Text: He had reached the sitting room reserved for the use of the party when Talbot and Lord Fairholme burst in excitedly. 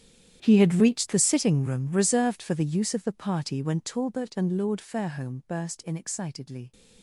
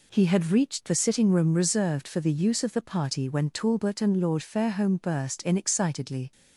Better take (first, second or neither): second